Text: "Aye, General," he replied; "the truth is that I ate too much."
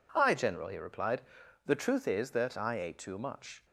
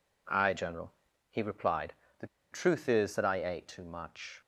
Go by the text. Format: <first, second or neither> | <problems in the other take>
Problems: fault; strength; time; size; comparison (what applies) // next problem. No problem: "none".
first | pauses between "the" and "truth"; slight; at 2.2 s; 0.26 s long